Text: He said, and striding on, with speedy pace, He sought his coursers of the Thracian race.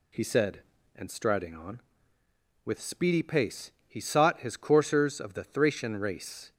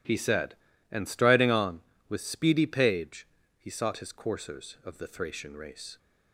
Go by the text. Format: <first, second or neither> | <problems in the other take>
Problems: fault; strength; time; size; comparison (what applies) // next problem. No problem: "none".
first | says "page" for "pace"; at 2.6 s